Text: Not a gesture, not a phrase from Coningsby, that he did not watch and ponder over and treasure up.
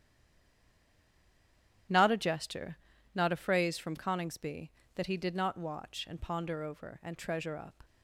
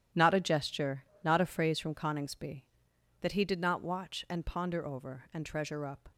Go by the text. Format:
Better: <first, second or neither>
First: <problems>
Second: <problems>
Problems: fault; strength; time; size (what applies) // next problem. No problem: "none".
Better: second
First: stays silent before the first word; noticeable; until 1.8 s; 1.8 s long // starts louder than the rest; strong; until 3.2 s; 11.5 dB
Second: starts louder than the rest; strong; until 1.3 s; 11 dB